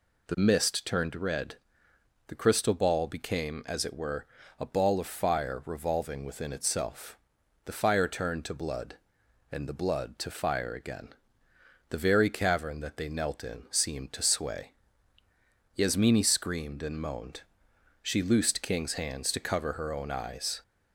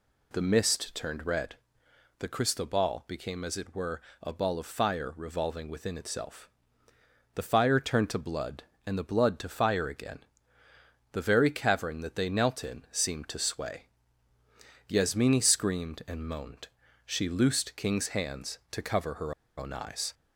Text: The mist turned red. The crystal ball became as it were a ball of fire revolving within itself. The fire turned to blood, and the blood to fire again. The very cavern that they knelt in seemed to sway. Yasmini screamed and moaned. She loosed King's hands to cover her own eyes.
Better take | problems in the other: first | pauses between "were" and "a"; slight; at 3.9 s; 0.22 s long; slight in the first // pauses between "her" and "own"; slight; at 19.3 s; 0.24 s long

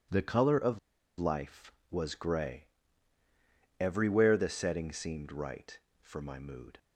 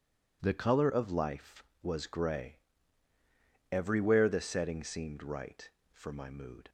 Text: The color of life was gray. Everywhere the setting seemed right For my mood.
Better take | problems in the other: second | pauses between "of" and "life"; at 0.7 s; 0.40 s long

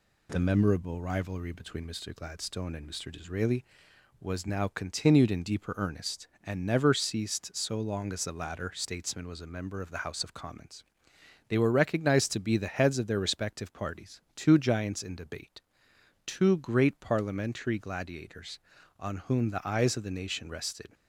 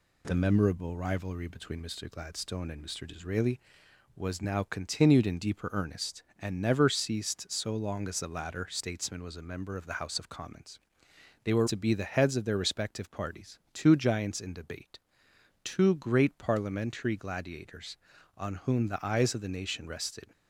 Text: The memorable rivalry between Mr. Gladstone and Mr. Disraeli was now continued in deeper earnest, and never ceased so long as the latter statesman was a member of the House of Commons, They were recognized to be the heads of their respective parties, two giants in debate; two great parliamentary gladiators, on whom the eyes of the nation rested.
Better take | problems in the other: first | skips "recognized"; at 11.6 s

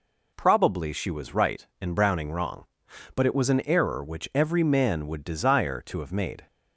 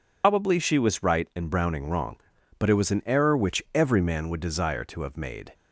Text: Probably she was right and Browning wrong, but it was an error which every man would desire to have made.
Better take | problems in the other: first | loses the start of "Probably"; at 0.2 s; 115 ms

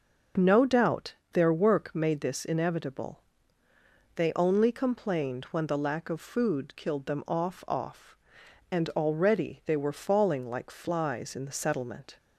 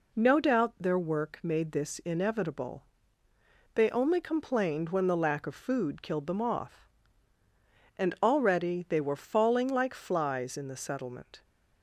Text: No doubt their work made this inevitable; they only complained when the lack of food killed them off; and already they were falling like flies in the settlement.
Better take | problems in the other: second | pauses between "doubt" and "their"; slight; at 1.1 s; 0.18 s long // says "off" twice; at 7.6 s

